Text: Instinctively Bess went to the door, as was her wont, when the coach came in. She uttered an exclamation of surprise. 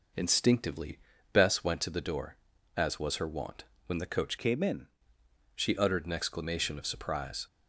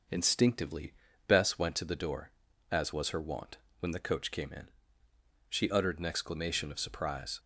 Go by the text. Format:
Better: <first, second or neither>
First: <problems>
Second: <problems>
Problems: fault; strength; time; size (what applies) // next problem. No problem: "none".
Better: second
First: pauses between "Instinctively" and "Bess"; slight; at 0.9 s; 0.34 s long // changes voice from "came" to "in"; from 4.3 to 4.8 s; 0.5 s long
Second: pauses between "Instinctively" and "Bess"; slight; at 0.9 s; 0.34 s long